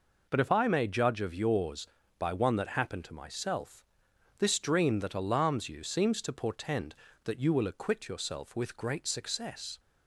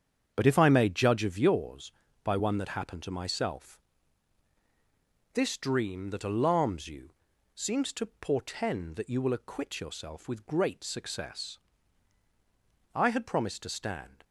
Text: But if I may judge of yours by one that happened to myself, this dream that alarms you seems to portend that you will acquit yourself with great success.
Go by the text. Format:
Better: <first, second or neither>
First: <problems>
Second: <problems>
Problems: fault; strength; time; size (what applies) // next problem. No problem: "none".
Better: first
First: none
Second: starts louder than the rest; strong; until 1.3 s; 7.5 dB // pauses between "you" and "seems"; at 7.1 s; 0.44 s long // goes on to say "I had promised to stand"; noticeable; from 12.9 s on; 1.3 s long